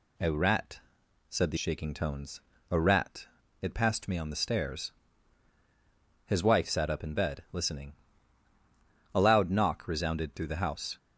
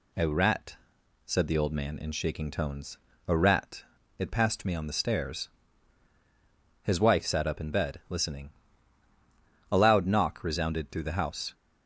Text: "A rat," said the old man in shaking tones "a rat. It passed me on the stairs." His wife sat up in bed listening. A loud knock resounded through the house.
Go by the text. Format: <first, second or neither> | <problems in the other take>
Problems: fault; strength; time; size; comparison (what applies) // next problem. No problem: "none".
second | skips "old man in"; at 1.5 s // pauses between "tones" and "a"; slight; at 2.4 s; 0.28 s long; slight in the second